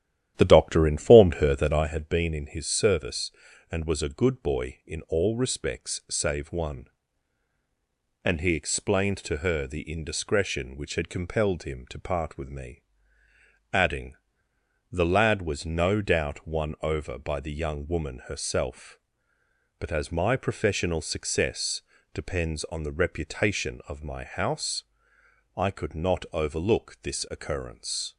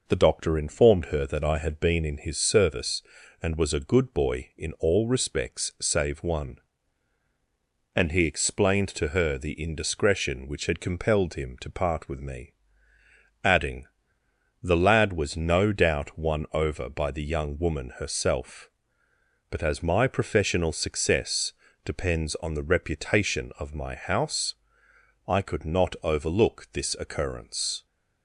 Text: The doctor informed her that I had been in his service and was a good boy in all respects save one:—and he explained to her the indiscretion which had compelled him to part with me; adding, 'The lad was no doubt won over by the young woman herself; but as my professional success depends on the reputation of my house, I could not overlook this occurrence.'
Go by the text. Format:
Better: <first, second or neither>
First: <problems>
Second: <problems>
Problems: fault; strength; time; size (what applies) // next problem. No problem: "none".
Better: second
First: starts louder than the rest; strong; until 1.9 s; 11.5 dB // pauses between "success" and "depends"; slight; at 21.8 s; 0.32 s long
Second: pauses between "success" and "depends"; slight; at 21.5 s; 0.32 s long